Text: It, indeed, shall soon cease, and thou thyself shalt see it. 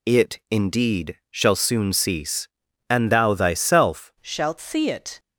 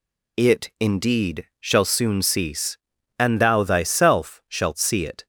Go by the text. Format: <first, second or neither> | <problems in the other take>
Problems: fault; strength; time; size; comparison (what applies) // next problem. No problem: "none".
second | changes voice at "shalt"; from 4.2 s on; 0.9 s long